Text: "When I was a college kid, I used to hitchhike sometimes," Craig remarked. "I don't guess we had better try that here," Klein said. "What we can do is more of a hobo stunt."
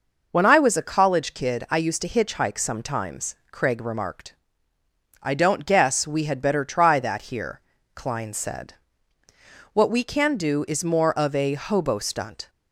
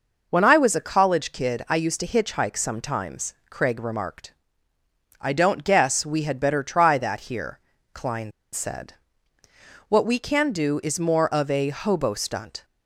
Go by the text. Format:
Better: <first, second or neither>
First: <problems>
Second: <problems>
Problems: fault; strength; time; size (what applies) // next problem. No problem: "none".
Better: first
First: none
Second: pauses between "Klein" and "said"; slight; at 8.3 s; 0.21 s long